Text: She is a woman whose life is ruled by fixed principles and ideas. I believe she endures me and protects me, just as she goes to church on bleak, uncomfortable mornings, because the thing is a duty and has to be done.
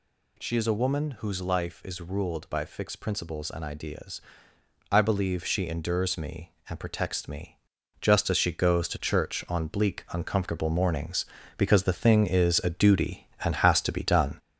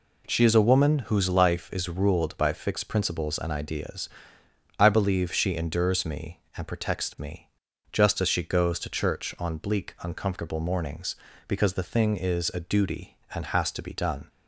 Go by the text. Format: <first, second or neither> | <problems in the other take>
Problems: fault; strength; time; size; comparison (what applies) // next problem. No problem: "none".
second | gets louder; noticeable; throughout; 4 dB